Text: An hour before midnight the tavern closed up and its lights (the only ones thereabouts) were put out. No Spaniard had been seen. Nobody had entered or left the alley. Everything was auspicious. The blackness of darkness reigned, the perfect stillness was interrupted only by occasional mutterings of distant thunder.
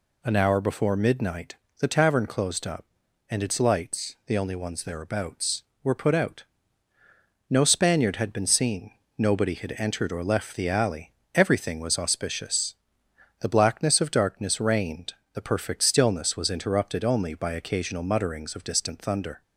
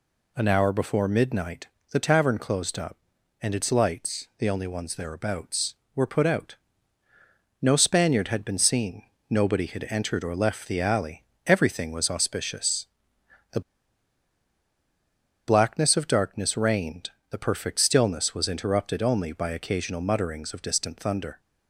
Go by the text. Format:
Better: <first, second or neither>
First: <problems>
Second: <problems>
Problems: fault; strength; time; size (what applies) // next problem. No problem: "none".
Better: first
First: pauses between "midnight" and "the"; slight; at 1.5 s; 0.24 s long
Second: pauses between "midnight" and "the"; slight; at 1.6 s; 0.24 s long // pauses between "The" and "blackness"; strong; at 13.5 s; 1.8 s long